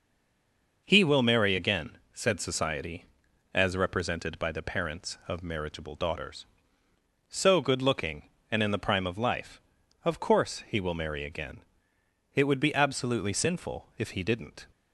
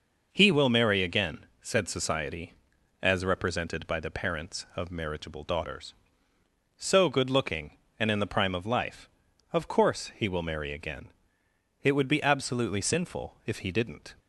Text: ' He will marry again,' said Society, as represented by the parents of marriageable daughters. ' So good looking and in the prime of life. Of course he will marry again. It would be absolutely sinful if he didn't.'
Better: second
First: stays silent before the first word; slight; until 0.8 s; 0.8 s long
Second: none

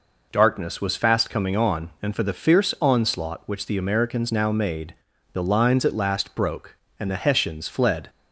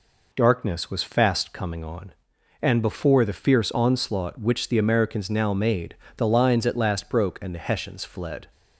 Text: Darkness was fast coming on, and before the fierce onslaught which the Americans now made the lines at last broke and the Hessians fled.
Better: second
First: says "for" for "before"; at 2.1 s // pauses between "made" and "the"; at 4.9 s; 0.38 s long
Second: pauses between "made" and "the"; slight; at 5.9 s; 0.22 s long

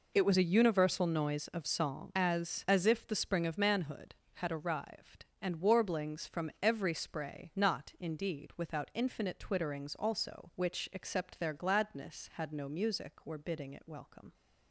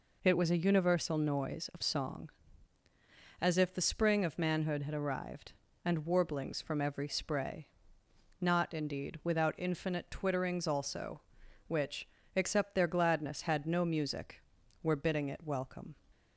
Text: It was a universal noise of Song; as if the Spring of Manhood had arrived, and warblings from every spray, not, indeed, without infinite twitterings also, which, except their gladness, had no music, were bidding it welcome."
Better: second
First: says "as" twice; at 2.6 s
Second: none

